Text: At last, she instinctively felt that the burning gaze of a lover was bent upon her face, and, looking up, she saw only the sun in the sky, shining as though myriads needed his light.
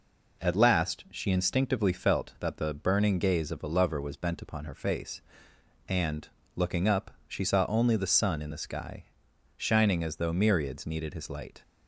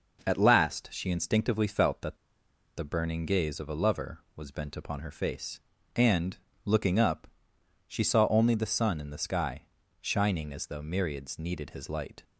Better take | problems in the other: first | pauses between "that" and "the"; noticeable; at 2.1 s; 0.61 s long

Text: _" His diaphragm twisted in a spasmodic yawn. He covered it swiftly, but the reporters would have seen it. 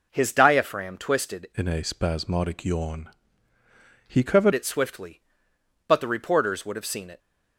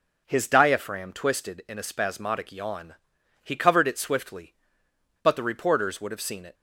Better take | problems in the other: second | changes voice from "in" to "covered"; from 1.5 to 4.5 s; 3.0 s long

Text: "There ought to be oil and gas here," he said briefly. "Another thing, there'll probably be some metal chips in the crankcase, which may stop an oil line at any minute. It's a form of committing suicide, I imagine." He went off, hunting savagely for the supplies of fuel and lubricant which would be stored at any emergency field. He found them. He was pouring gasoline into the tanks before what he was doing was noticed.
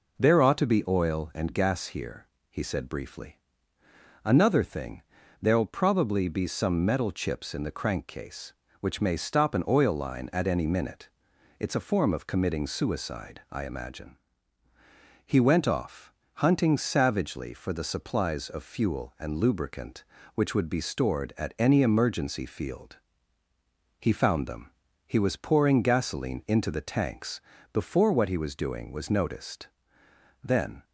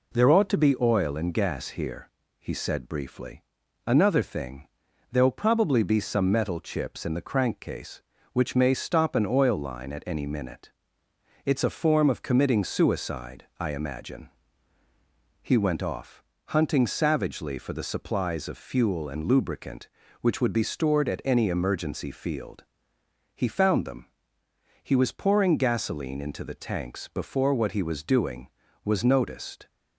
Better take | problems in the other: second | pauses between "tanks" and "before"; slight; at 27.4 s; 0.32 s long // goes on to say "Then"; slight; from 30.4 s on; 0.40 s long

